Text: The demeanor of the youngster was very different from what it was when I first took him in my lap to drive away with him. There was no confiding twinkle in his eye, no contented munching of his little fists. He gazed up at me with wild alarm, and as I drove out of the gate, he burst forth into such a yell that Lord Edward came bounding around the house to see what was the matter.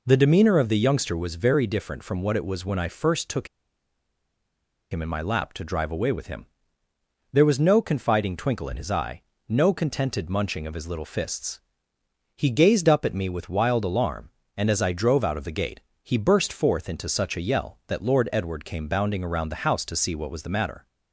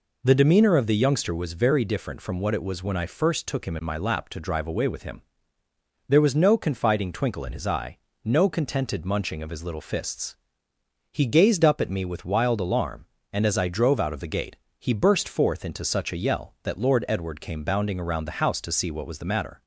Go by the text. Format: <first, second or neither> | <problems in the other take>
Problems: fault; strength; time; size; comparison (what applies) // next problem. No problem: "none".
second | pauses between "took" and "him"; strong; at 3.4 s; 1.4 s long